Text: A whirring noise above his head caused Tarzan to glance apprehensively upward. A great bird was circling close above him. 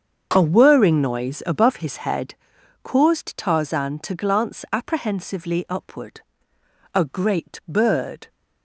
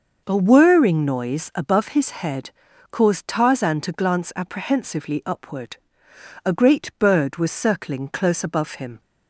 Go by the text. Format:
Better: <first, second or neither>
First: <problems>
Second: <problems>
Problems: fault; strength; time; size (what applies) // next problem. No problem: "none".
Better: second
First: starts louder than the rest; until 1.3 s; 7 dB // pauses between "head" and "caused"; noticeable; at 2.3 s; 0.48 s long // stops before "was circling close above him"; at 8.2 s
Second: pauses between "head" and "caused"; at 2.5 s; 0.40 s long